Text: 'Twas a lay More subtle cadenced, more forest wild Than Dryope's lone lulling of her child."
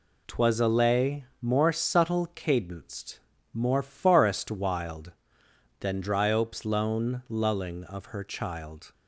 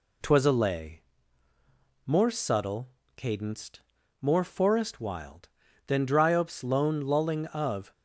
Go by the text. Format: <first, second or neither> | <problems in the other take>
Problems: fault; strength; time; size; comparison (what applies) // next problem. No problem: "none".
first | pauses between "lay" and "More"; at 1.0 s; 1.0 s long; slight in the first // pauses between "subtle" and "cadenced"; slight; at 2.8 s; 0.26 s long // stops before "her child"; at 7.9 s